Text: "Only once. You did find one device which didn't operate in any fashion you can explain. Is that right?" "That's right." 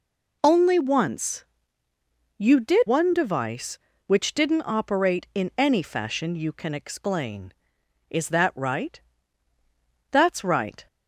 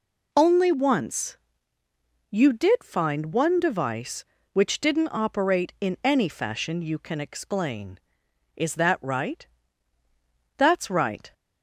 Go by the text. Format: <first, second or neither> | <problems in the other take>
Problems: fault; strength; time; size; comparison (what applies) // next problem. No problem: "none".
second | skips "find"; at 2.8 s